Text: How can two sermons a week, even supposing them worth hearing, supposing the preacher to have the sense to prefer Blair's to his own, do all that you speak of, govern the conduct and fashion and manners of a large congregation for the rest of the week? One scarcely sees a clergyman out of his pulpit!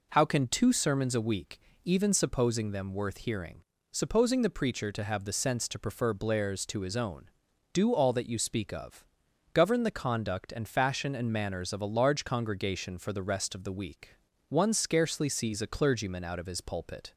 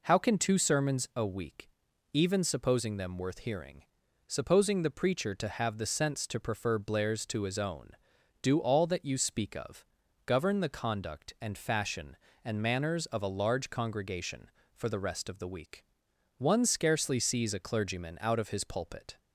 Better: neither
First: none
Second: none

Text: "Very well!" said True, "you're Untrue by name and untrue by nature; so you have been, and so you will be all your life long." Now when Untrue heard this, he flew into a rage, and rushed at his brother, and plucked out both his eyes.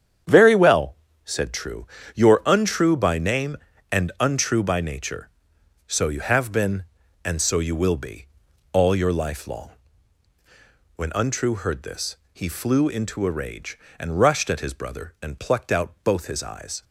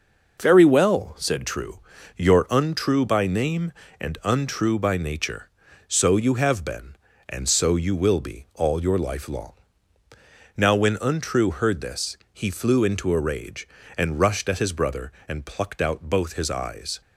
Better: second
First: starts louder than the rest; strong; until 1.5 s; 8.5 dB // pauses between "be" and "all"; at 8.2 s; 0.44 s long // skips "Now"; at 10.3 s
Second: none

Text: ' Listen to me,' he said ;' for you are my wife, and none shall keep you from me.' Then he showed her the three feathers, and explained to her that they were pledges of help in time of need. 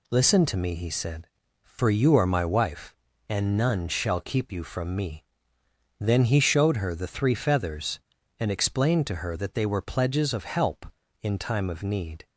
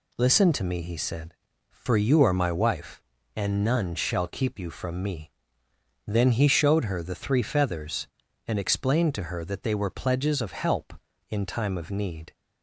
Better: neither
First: none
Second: none

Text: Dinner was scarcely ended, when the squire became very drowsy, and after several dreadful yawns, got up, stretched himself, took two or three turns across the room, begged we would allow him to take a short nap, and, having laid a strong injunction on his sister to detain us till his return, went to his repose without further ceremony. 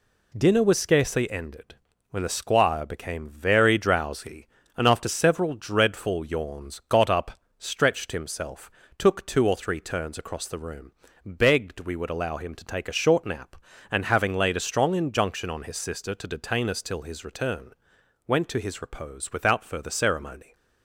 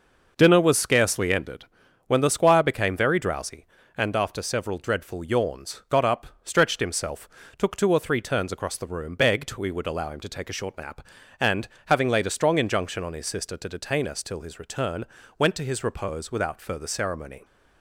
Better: neither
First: none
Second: none

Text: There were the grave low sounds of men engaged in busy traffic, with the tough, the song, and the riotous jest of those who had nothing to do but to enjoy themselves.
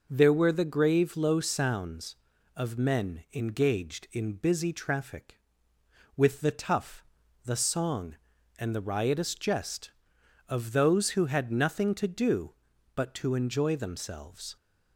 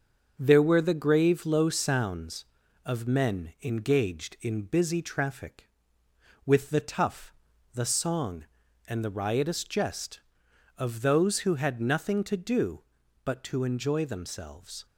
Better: first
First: none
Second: gets quieter; noticeable; throughout; 5 dB

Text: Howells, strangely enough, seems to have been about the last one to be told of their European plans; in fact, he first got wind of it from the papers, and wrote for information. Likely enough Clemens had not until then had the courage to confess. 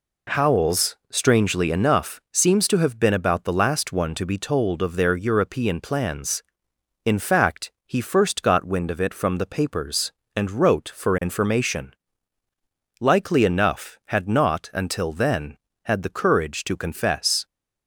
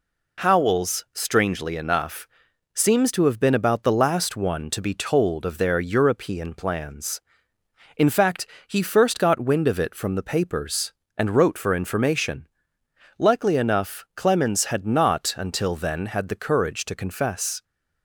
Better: second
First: skips "Clemens"; at 14.0 s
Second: none

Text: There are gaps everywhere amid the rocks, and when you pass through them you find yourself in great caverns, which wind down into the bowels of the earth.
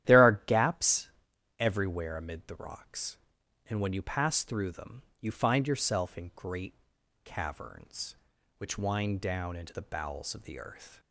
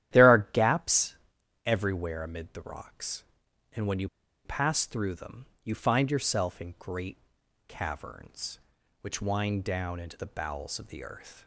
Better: first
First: starts louder than the rest; strong; until 1.6 s; 12 dB // pauses between "gaps" and "everywhere"; noticeable; at 1.0 s; 0.48 s long // pauses between "them" and "you"; slight; at 5.0 s; 0.18 s long // pauses between "great" and "caverns"; noticeable; at 6.7 s; 0.50 s long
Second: starts louder than the rest; strong; until 1.6 s; 12 dB // pauses between "gaps" and "everywhere"; noticeable; at 1.1 s; 0.48 s long // pauses between "you" and "pass"; at 4.0 s; 0.36 s long // pauses between "them" and "you"; slight; at 5.4 s; 0.18 s long // pauses between "great" and "caverns"; noticeable; at 7.1 s; 0.50 s long

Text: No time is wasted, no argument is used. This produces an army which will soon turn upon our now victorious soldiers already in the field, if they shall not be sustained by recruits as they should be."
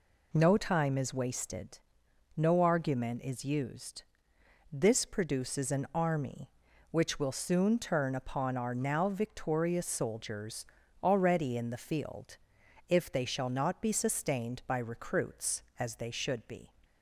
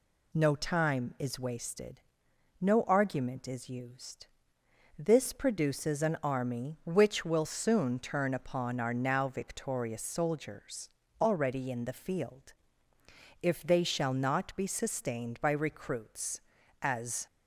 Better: first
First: pauses between "soldiers" and "already"; slight; at 10.6 s; 0.36 s long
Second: pauses between "soldiers" and "already"; slight; at 10.8 s; 0.32 s long // stops before "they should be"; at 17.2 s

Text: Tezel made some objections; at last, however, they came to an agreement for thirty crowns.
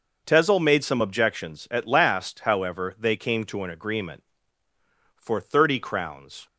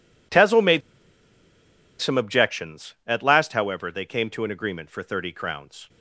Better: first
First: none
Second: pauses between "made" and "some"; at 0.8 s; 1.1 s long

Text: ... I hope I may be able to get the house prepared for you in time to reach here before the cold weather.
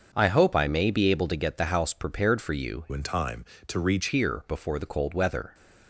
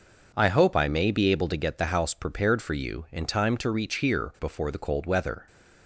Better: second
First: starts louder than the rest; until 1.1 s; 6.5 dB // changes voice from "in" to "reach"; from 2.9 to 4.0 s; 1.1 s long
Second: none

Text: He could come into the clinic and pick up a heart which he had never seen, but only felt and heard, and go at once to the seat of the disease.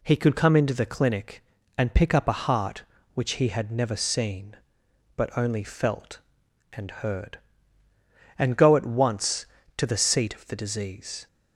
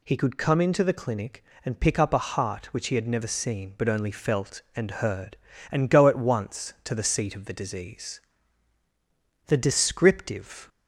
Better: first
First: none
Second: goes on to say "The descriptive"; noticeable; from 9.4 s on; 1.2 s long

